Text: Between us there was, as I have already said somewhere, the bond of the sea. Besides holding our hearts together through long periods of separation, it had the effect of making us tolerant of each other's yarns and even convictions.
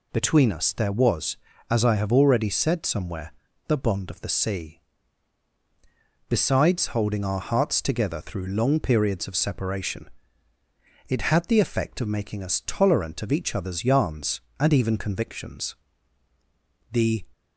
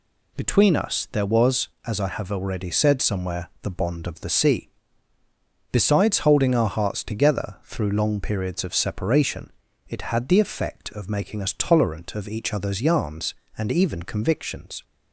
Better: second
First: goes on to say "The"; slight; from 16.9 s on; 0.36 s long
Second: none

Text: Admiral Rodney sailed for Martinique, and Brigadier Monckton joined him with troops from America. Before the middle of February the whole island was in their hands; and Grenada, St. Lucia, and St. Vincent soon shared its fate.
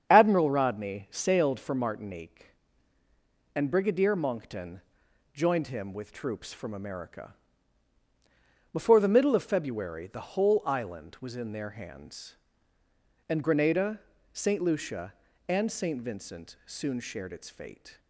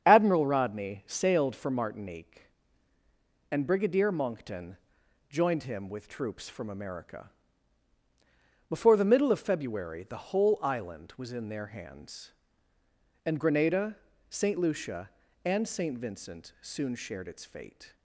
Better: neither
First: starts louder than the rest; strong; until 1.1 s; 7.5 dB // pauses between "Monckton" and "joined"; noticeable; at 4.8 s; 0.50 s long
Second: starts louder than the rest; strong; until 1.0 s; 8 dB // pauses between "Monckton" and "joined"; noticeable; at 4.7 s; 0.50 s long

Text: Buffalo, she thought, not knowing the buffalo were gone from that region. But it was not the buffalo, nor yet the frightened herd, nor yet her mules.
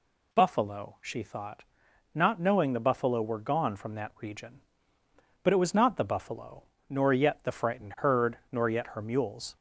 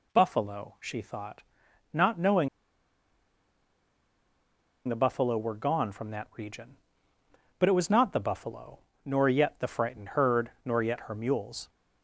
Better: first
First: none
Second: pauses between "knowing" and "the"; strong; at 2.4 s; 2.3 s long

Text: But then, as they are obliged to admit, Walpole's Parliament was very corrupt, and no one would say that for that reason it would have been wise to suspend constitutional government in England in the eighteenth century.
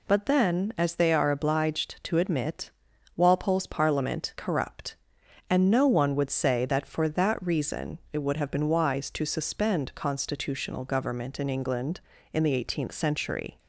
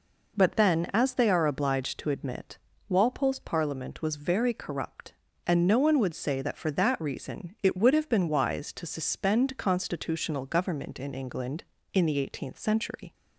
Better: second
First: skips "was very"; at 4.3 s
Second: none

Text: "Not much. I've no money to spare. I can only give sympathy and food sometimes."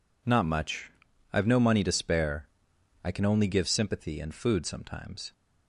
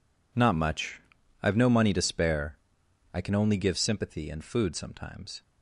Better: first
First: none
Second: gets quieter; strong; throughout; 15 dB

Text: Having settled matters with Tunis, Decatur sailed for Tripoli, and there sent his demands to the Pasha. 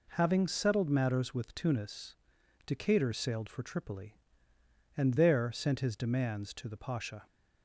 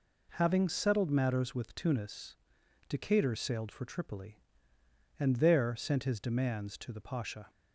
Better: neither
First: none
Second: none

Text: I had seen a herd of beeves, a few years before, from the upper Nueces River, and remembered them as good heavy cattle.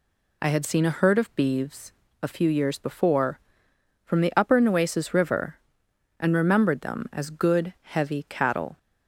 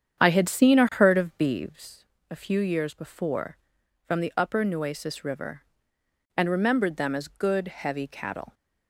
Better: first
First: none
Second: starts louder than the rest; strong; until 1.8 s; 8.5 dB

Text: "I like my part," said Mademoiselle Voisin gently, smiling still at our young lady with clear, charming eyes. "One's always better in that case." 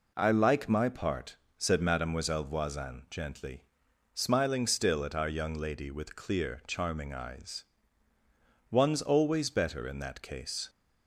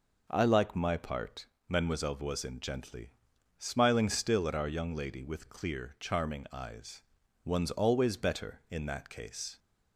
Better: first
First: none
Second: skips "said"; at 1.5 s

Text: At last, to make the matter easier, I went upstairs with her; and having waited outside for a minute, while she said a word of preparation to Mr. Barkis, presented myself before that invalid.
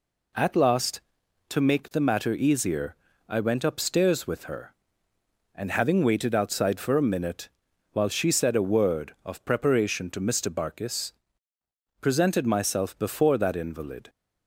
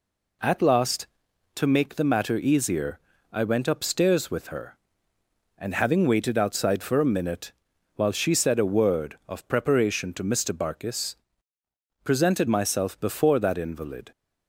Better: neither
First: none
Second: none

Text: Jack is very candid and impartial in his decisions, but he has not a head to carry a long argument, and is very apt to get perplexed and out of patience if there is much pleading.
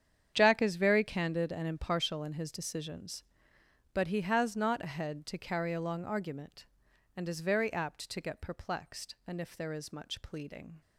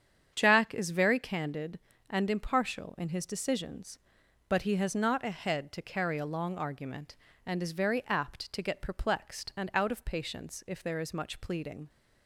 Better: second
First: starts louder than the rest; strong; until 1.3 s; 8.5 dB // skips "out of patience"; at 9.4 s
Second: starts louder than the rest; strong; until 1.3 s; 8 dB

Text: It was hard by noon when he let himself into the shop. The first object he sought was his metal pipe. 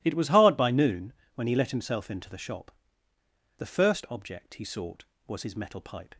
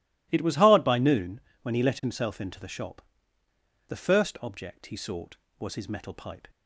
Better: neither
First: pauses between "noon" and "when"; slight; at 1.1 s; 0.22 s long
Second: pauses between "noon" and "when"; slight; at 1.3 s; 0.22 s long

